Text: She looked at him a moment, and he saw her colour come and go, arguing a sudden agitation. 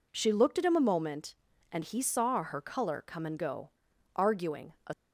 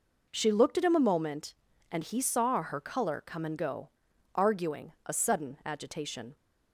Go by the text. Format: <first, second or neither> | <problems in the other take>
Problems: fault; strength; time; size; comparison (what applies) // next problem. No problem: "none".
second | stops before "sudden agitation"; at 4.9 s